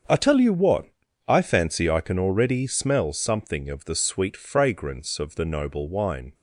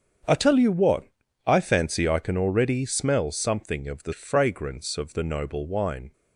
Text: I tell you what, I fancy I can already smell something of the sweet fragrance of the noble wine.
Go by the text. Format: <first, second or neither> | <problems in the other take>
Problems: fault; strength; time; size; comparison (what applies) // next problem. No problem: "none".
first | starts louder than the rest; strong; until 1.6 s; 7.5 dB; also in the first // skips "sweet"; at 4.1 s